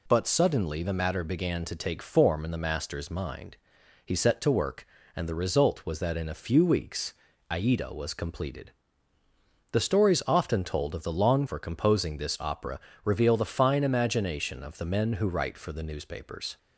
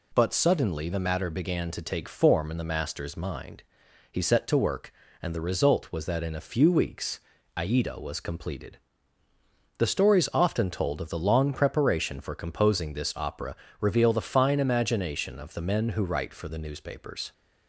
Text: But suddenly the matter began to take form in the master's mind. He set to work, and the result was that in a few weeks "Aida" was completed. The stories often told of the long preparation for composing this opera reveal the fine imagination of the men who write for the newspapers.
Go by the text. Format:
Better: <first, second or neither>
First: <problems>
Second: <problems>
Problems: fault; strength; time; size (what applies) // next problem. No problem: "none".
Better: second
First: pauses between "weeks" and "Aida"; at 7.1 s; 0.38 s long // skips "preparation"; at 11.4 s // pauses between "opera" and "reveal"; slight; at 12.7 s; 0.26 s long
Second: pauses between "weeks" and "Aida"; at 7.1 s; 0.38 s long // pauses between "opera" and "reveal"; slight; at 13.5 s; 0.26 s long